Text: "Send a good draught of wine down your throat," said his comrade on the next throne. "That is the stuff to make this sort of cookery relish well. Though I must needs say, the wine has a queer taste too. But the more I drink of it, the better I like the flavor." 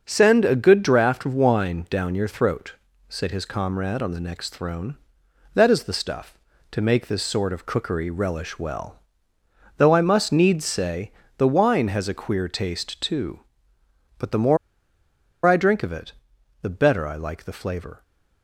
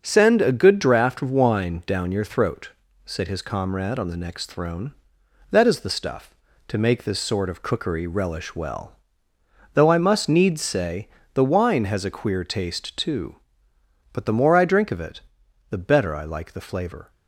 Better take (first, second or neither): second